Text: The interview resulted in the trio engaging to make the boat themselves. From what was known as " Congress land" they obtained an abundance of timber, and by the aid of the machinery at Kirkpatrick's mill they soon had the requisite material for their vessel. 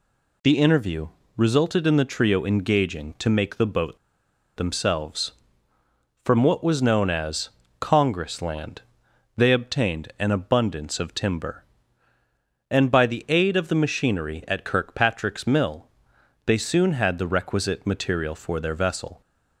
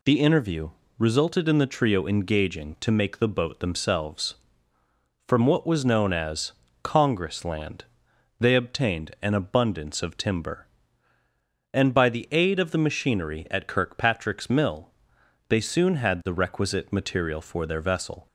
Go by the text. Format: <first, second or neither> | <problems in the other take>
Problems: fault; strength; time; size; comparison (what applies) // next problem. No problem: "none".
second | pauses between "interview" and "resulted"; slight; at 1.0 s; 0.26 s long; slight in the second // pauses between "boat" and "themselves"; noticeable; at 3.9 s; 0.58 s long // pauses between "land" and "they"; noticeable; at 8.8 s; 0.56 s long; noticeable in the second // pauses between "mill" and "they"; noticeable; at 15.8 s; 0.60 s long; noticeable in the second